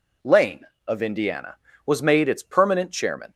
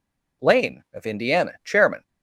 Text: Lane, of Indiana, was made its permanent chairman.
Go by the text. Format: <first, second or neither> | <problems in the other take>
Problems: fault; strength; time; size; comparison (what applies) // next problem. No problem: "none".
first | skips "was made its permanent"; at 1.6 s